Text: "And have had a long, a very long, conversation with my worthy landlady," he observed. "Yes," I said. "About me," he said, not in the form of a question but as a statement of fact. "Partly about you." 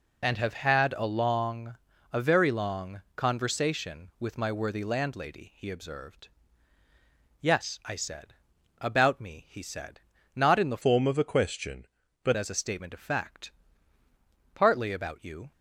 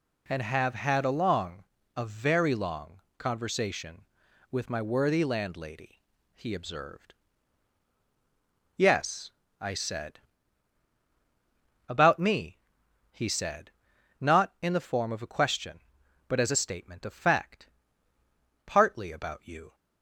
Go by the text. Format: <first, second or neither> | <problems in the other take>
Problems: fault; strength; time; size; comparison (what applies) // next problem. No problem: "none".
second | changes voice from "form" to "but"; from 10.8 to 12.3 s; 1.5 s long